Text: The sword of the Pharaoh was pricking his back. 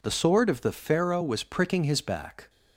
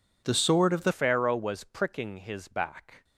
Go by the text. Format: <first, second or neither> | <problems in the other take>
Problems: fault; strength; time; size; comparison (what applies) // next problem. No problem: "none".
first | changes voice at "Pharaoh"; from 0.9 s on; 2.1 s long